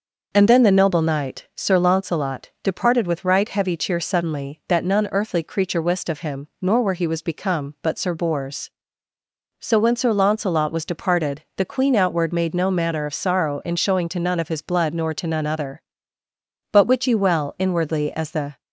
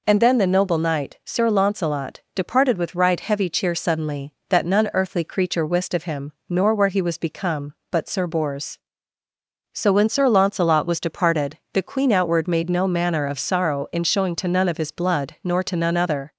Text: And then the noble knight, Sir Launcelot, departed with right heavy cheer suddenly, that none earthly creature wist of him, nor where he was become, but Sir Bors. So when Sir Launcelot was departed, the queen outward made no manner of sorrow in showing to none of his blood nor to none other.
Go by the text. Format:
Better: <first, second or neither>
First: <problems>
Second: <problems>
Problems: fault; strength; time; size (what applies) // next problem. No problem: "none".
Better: second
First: goes on to say "But wit ye well inwardly as the"; strong; from 16.7 s on; 1.9 s long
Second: none